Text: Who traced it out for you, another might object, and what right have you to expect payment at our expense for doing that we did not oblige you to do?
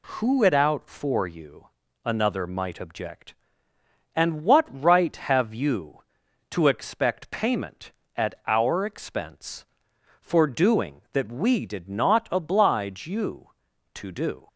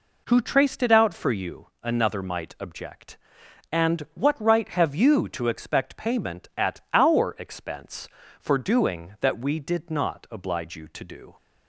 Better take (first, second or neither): second